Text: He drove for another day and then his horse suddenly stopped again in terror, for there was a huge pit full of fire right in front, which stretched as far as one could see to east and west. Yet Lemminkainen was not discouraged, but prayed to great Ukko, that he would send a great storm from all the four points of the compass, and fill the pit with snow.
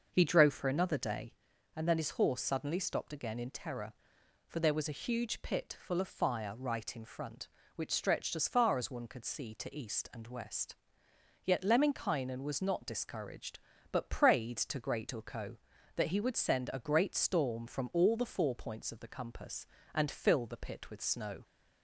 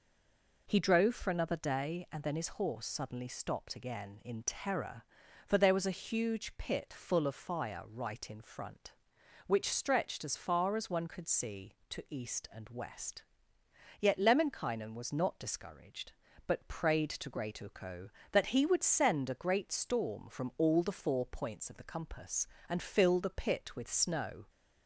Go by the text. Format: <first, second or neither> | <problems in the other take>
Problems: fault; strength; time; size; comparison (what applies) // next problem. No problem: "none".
first | stays silent before the first word; slight; until 0.6 s; 0.6 s long